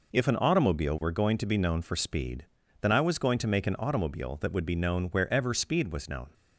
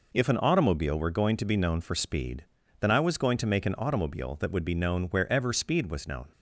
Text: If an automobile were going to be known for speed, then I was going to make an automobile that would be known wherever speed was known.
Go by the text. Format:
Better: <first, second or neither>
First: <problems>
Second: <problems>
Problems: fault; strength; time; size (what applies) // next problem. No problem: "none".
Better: neither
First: none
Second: none